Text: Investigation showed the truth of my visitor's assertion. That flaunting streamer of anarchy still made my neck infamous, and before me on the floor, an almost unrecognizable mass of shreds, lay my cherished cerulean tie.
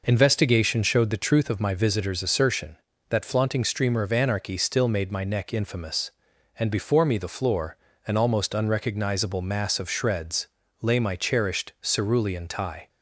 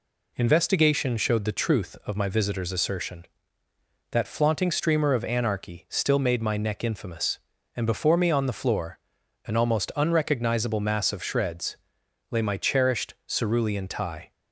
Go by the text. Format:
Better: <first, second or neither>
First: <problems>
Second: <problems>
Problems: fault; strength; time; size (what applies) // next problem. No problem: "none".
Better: second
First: skips "on"; at 7.1 s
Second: none